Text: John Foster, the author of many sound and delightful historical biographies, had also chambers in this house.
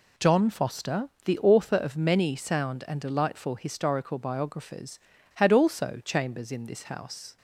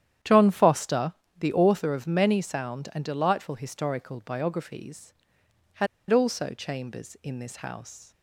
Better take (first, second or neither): first